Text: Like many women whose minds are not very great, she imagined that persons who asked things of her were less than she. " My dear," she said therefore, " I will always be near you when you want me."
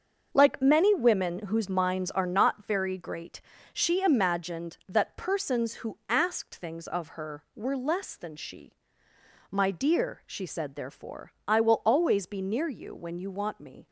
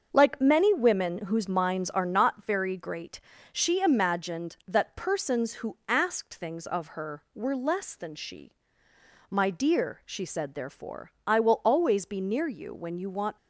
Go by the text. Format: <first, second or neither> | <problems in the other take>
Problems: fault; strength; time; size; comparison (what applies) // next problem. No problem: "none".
first | starts louder than the rest; until 1.1 s; 7 dB; also in the first // stops before "me"; at 13.3 s